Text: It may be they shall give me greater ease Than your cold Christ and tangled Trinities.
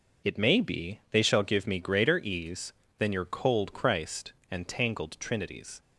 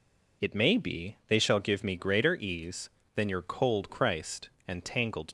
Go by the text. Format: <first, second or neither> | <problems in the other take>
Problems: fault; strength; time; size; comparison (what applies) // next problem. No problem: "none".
first | stops before "Trinities"; at 5.2 s